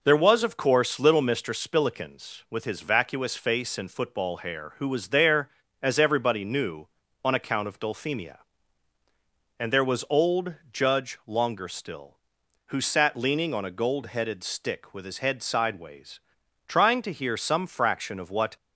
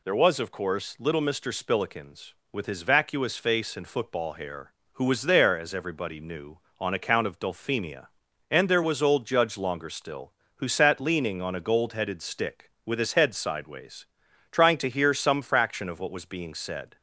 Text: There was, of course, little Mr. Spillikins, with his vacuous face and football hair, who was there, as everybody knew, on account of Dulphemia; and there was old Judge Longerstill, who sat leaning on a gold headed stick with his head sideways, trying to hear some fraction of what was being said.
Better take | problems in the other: second | pauses between "old" and "Judge"; slight; at 10.5 s; 0.18 s long // stops before "was being said"; at 18.5 s

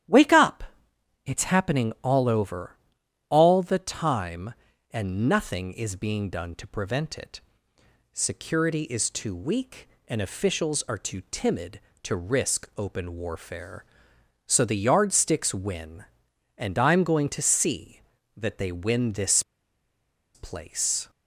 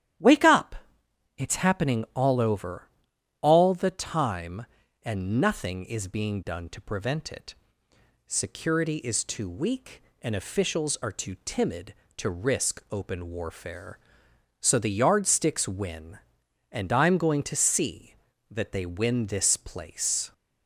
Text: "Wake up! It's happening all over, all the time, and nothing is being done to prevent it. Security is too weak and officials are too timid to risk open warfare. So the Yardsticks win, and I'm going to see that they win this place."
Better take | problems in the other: second | starts louder than the rest; strong; until 1.6 s; 11 dB; strong in the second // pauses between "this" and "place"; noticeable; at 19.4 s; 0.94 s long

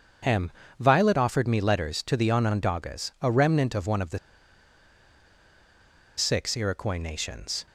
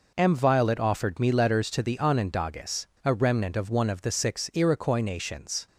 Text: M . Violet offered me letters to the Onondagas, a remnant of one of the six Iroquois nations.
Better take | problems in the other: second | starts louder than the rest; strong; until 1.5 s; 7 dB // pauses between "the" and "six"; strong; at 4.1 s; 1.9 s long

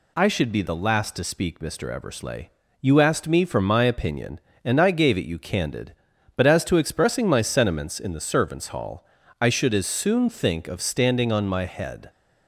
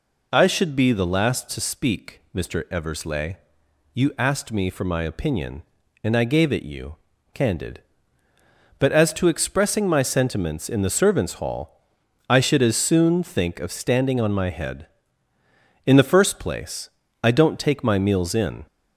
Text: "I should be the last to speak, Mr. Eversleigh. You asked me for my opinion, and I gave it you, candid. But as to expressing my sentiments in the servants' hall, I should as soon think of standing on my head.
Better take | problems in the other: first | goes on to say "In the first place I don't take my meals in"; strong; from 15.8 s on; 2.8 s long

